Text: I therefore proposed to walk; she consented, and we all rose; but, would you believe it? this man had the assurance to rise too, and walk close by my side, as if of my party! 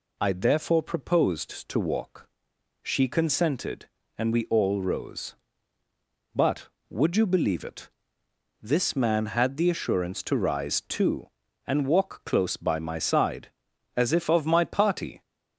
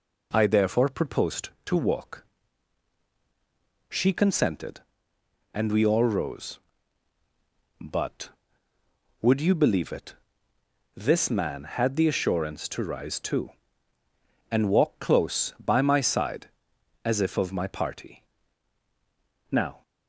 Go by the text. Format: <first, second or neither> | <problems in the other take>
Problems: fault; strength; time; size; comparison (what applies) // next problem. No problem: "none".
first | goes on to say "Now"; slight; from 19.5 s on; 0.30 s long